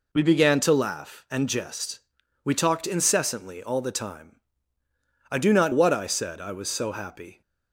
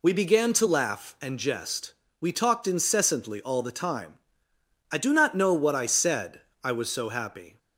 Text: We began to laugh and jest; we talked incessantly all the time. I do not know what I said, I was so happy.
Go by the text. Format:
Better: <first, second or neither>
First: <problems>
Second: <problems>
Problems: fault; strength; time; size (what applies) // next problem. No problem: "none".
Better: second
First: skips "know"; at 5.7 s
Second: none